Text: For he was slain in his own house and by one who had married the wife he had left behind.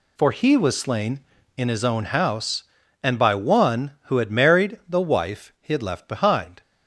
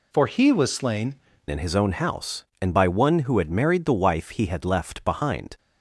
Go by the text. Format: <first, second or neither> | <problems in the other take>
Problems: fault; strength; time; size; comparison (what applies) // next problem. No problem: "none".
first | changes voice at "in"; from 1.4 s on; 4.1 s long